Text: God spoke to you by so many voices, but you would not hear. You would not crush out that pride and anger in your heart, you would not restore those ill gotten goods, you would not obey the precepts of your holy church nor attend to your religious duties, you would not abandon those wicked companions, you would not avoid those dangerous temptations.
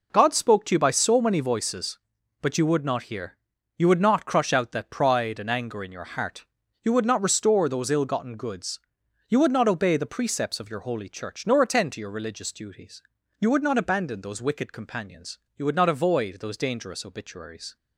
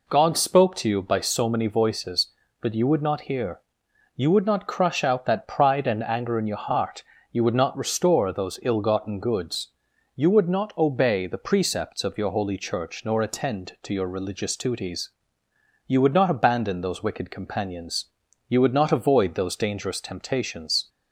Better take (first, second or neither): second